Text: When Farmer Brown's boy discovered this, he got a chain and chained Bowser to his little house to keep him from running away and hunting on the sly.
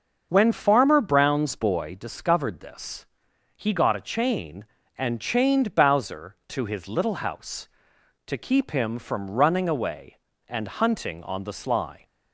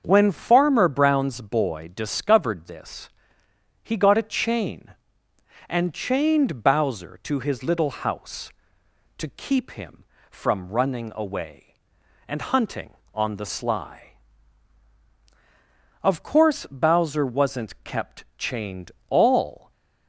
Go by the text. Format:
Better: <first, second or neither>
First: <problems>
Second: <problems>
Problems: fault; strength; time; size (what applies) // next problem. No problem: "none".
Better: first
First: starts louder than the rest; until 1.3 s; 6.5 dB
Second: starts louder than the rest; until 1.0 s; 7 dB // goes on to say "Of course Bowser wasn't kept chained all"; strong; from 16.0 s on; 3.6 s long